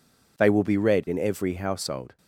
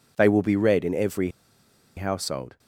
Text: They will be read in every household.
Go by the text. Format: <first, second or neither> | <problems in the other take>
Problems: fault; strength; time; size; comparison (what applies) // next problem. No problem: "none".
first | pauses between "every" and "household"; noticeable; at 1.3 s; 0.65 s long